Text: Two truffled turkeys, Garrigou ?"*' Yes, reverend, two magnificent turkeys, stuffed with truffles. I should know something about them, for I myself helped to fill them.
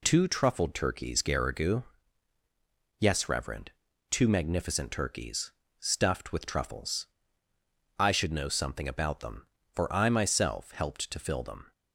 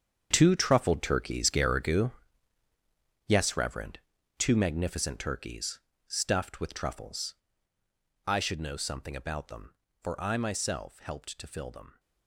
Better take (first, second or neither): first